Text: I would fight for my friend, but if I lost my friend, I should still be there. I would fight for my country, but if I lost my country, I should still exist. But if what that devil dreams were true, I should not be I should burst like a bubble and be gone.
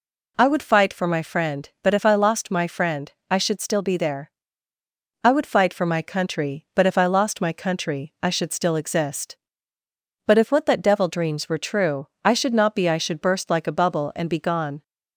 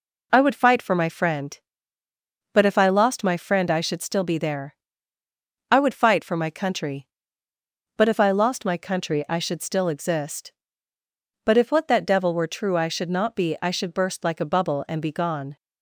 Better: first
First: none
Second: skips "dreams"; at 12.3 s

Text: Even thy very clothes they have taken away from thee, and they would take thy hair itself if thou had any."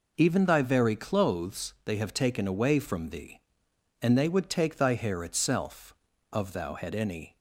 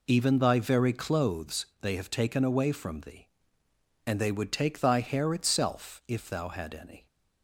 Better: second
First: says "of" for "if"; at 6.3 s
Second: none

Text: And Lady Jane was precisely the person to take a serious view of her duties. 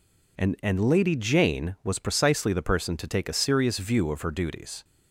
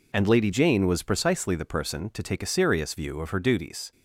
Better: second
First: says "And" twice; at 0.6 s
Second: none

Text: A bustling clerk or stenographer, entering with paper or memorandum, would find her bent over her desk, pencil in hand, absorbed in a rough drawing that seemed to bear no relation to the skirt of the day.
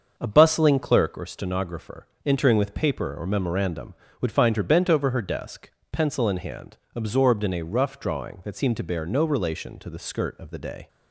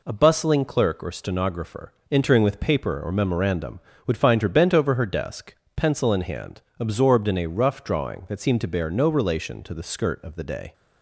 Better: second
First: starts louder than the rest; until 1.2 s; 6.5 dB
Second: none

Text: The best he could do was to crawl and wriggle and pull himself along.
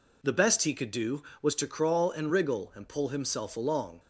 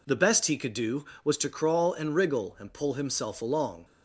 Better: neither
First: none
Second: none

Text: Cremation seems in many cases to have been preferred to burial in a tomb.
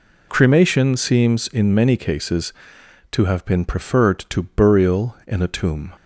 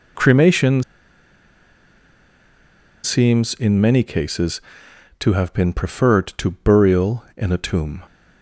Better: first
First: none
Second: pauses between "Cremation" and "seems"; strong; at 0.8 s; 2.2 s long

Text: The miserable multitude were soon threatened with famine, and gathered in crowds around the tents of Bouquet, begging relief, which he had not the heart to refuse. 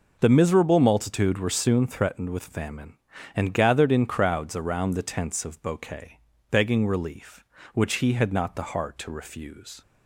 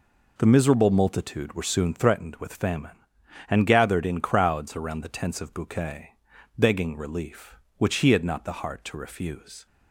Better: neither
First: none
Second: none

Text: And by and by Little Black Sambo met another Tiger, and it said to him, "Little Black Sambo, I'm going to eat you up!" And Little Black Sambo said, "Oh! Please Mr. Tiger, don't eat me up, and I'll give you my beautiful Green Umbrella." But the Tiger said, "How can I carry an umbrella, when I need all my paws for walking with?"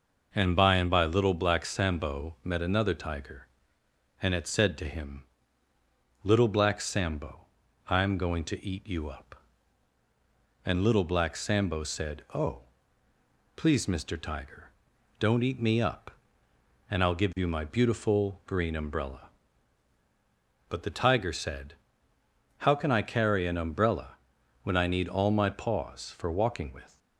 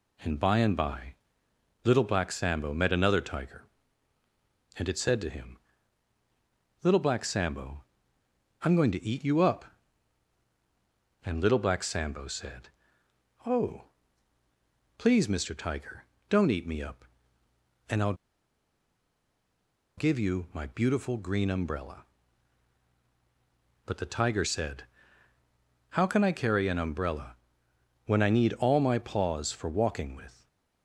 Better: first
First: none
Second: pauses between "by" and "Little"; noticeable; at 1.1 s; 0.70 s long // pauses between "I'll" and "give"; strong; at 18.1 s; 1.8 s long // stays silent after the last word; slight; from 30.3 s on; 0.5 s long

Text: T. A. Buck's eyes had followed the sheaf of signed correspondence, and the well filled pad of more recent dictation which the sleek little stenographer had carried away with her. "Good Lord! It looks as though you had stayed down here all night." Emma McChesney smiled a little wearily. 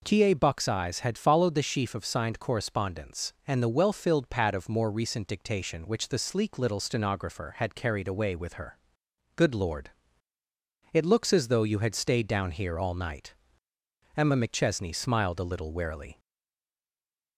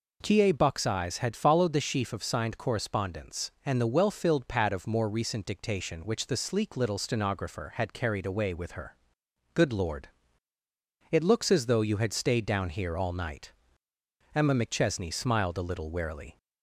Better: second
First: stays silent after the last word; noticeable; from 16.1 s on; 1.2 s long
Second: none

